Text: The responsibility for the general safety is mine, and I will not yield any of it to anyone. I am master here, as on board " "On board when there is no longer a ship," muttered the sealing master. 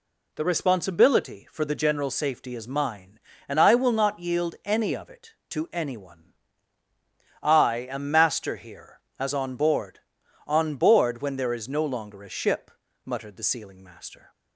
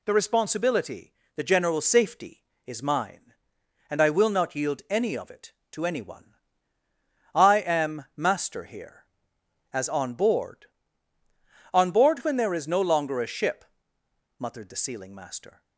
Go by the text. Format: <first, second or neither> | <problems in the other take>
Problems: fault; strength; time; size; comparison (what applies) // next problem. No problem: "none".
first | skips "for"; at 1.2 s